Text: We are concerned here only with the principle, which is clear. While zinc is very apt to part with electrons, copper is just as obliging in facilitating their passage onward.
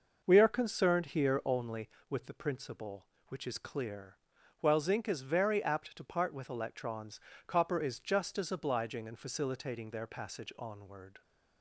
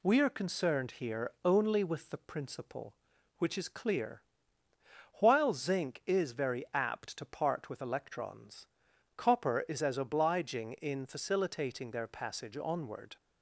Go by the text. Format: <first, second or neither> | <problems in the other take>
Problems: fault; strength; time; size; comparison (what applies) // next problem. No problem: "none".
first | skips "just"; at 9.8 s